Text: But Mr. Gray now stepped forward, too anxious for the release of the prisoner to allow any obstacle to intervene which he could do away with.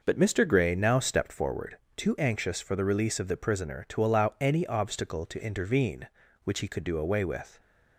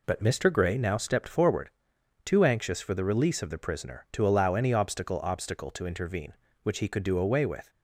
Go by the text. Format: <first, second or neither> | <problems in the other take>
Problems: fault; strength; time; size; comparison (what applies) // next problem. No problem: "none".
first | says "obstacle" twice; at 5.2 s